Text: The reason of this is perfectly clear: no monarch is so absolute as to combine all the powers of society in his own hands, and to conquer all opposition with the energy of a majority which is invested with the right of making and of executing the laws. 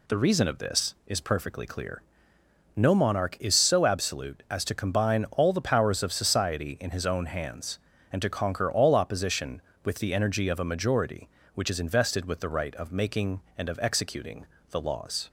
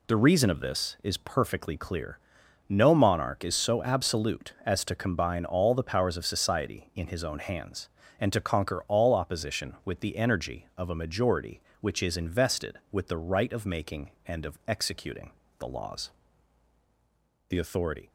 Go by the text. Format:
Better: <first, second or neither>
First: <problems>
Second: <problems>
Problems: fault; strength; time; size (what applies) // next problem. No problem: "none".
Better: first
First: pauses between "executing" and "the"; slight; at 14.4 s; 0.26 s long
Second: pauses between "executing" and "the"; slight; at 15.3 s; 0.28 s long // goes on to say "The authority"; noticeable; from 17.4 s on; 0.62 s long